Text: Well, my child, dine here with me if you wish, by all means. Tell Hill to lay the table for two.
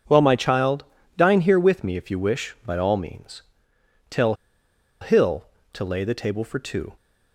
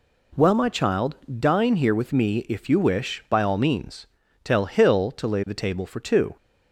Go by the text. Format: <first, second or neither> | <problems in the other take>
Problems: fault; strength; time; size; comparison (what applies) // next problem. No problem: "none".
second | pauses between "Tell" and "Hill"; noticeable; at 4.3 s; 0.65 s long